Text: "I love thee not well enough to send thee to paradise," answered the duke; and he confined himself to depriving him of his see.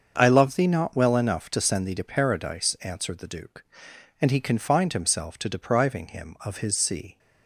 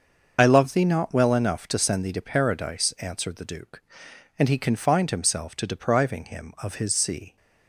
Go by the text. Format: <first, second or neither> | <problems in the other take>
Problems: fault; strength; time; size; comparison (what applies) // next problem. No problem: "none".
first | loses the start of "I"; at 0.3 s; 55 ms // starts louder than the rest; until 1.3 s; 6.5 dB; also in the first